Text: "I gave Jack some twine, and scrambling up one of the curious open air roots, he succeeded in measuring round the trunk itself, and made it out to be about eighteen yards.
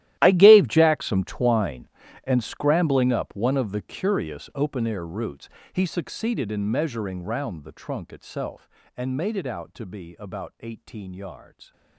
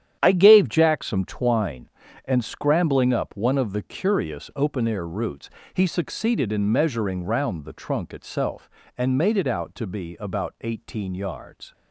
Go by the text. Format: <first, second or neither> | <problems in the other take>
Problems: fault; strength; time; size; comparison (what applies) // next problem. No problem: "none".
second | gets quieter; strong; throughout; 18 dB // starts louder than the rest; strong; until 1.2 s; 13.5 dB; strong in the second